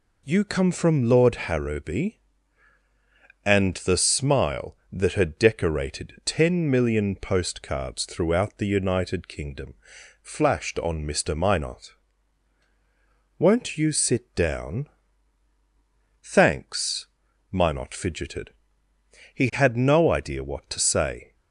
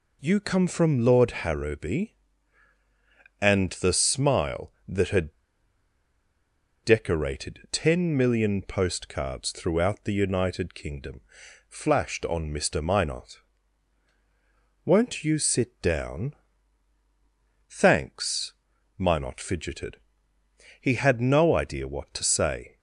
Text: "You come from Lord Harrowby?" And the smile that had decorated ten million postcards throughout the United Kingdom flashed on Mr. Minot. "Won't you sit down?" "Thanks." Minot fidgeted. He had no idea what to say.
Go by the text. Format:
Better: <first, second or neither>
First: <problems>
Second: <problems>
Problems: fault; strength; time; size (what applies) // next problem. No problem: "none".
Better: first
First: pauses between "Kingdom" and "flashed"; noticeable; at 9.7 s; 0.48 s long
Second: pauses between "had" and "decorated"; strong; at 5.3 s; 1.5 s long // pauses between "Kingdom" and "flashed"; noticeable; at 11.1 s; 0.48 s long